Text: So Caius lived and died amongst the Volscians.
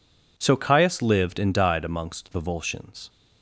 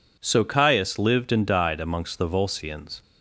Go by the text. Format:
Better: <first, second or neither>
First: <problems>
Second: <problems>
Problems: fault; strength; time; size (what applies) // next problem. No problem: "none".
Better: neither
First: none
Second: none